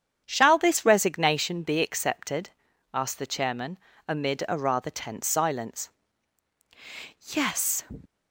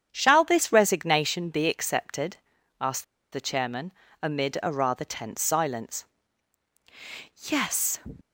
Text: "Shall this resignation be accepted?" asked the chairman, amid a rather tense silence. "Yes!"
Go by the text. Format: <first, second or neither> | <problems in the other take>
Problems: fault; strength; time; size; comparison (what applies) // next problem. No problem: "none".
first | starts louder than the rest; strong; until 1.1 s; 8 dB; strong in the first // pauses between "asked" and "the"; slight; at 3.0 s; 0.28 s long